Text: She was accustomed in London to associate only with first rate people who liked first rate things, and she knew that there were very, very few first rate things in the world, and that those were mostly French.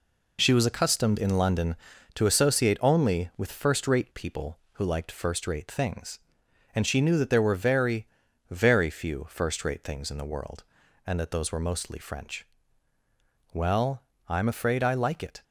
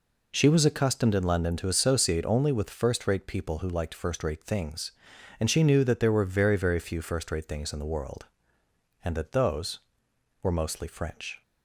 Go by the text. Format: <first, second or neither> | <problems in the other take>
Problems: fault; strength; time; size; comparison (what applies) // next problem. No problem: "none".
second | goes on to say "Well I'm afraid I like it"; strong; from 13.5 s on; 1.9 s long